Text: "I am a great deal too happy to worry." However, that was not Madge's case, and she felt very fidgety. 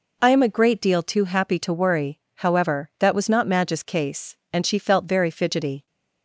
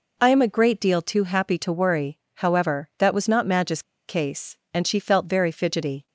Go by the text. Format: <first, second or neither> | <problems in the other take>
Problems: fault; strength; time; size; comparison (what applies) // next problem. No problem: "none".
first | pauses between "Madge's" and "case"; slight; at 3.8 s; 0.23 s long